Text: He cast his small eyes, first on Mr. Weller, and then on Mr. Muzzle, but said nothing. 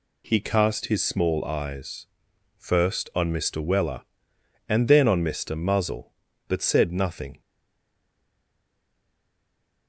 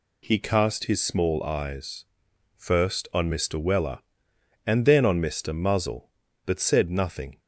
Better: second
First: stays silent after the last word; from 7.4 s on; 2.4 s long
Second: none

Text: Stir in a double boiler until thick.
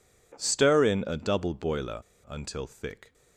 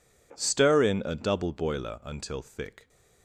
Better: second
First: pauses between "boiler" and "until"; slight; at 2.0 s; 0.26 s long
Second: none

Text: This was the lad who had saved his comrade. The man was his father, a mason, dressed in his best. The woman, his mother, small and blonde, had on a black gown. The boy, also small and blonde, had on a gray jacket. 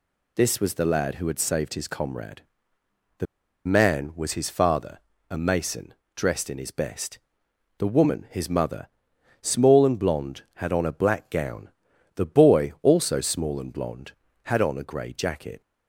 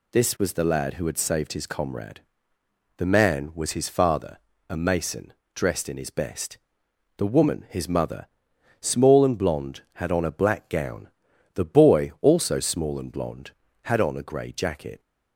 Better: second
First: pauses between "The" and "man"; at 3.2 s; 0.40 s long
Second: none

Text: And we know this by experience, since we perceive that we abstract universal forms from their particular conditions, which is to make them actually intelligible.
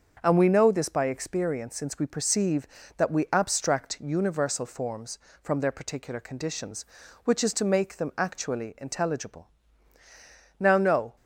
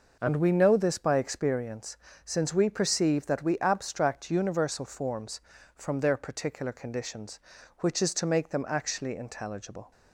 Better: second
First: starts louder than the rest; until 1.2 s; 6.5 dB // goes on to say "Now no"; from 10.5 s on; 0.56 s long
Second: none

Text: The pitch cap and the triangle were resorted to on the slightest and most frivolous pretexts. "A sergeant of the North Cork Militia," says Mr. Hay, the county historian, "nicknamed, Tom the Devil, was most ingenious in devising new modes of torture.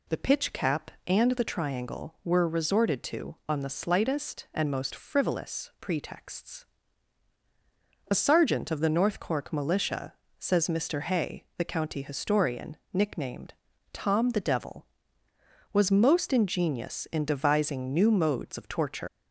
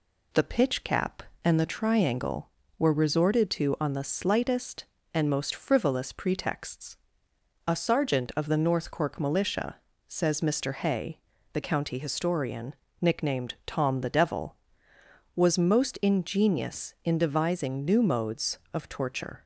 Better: second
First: leaves "torture" unfinished; at 19.0 s; 175 ms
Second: none

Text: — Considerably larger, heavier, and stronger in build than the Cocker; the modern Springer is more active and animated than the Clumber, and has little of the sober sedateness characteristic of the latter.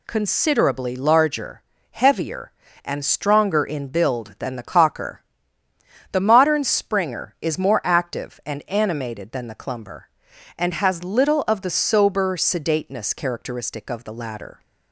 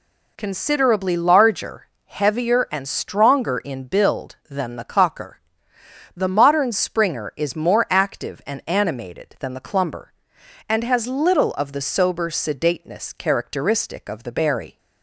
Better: first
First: none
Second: says "berry" for "latter"; at 14.3 s

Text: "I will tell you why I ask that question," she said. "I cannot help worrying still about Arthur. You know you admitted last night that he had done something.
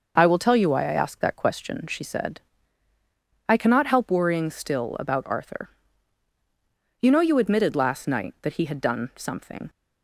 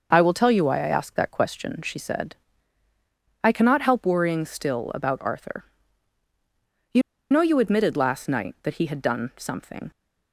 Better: first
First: none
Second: starts louder than the rest; noticeable; until 1.1 s; 6 dB // pauses between "You" and "know"; slight; at 7.0 s; 0.29 s long

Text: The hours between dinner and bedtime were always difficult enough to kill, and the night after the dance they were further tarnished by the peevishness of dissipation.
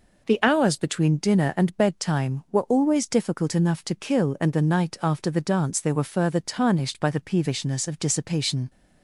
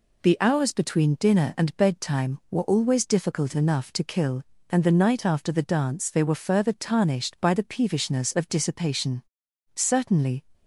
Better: first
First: none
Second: goes on to say "Certainly"; noticeable; from 9.7 s on; 0.68 s long

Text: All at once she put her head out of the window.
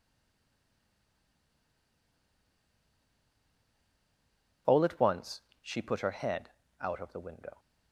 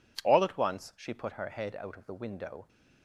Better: second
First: stays silent before the first word; strong; until 4.6 s; 4.6 s long // pauses between "once" and "she"; slight; at 5.4 s; 0.18 s long // pauses between "head" and "out"; slight; at 6.4 s; 0.32 s long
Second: none

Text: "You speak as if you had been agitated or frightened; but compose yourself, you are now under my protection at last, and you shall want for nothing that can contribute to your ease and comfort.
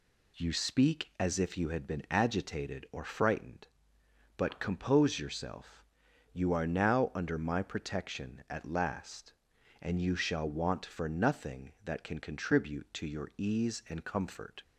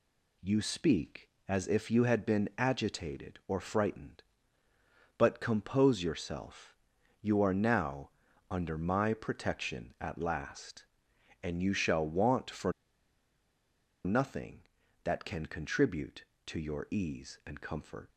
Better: first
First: none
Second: pauses between "now" and "under"; at 8.1 s; 0.38 s long // pauses between "for" and "nothing"; strong; at 12.7 s; 1.3 s long

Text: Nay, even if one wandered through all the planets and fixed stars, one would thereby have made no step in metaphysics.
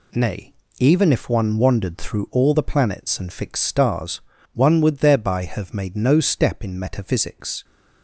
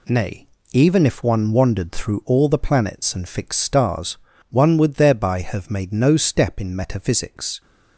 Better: neither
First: none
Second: none

